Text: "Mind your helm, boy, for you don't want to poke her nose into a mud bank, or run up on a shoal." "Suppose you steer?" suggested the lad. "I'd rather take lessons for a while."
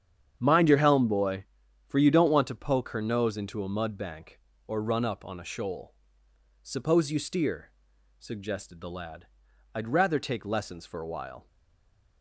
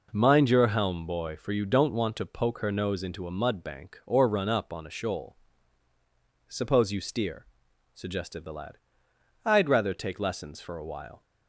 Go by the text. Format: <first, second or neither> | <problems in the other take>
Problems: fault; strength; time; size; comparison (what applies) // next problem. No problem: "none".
second | starts louder than the rest; strong; until 1.3 s; 8.5 dB // stays silent after the last word; slight; from 11.4 s on; 0.8 s long